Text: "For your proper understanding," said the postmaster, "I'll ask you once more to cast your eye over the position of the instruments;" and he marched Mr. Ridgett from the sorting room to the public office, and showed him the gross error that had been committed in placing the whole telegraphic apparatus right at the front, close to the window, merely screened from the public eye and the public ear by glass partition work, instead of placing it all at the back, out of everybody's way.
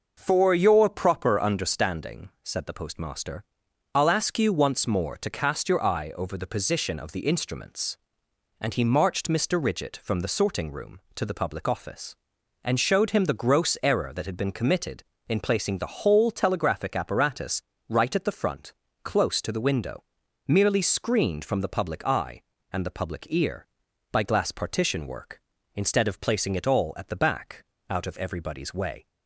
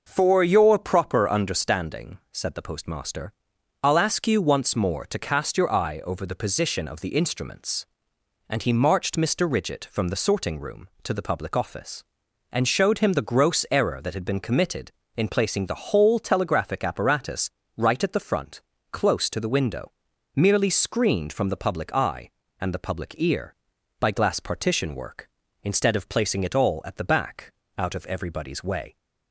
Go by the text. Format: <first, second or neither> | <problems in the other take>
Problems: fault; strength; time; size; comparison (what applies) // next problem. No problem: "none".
neither | pauses between "apparatus" and "right"; slight; the same in both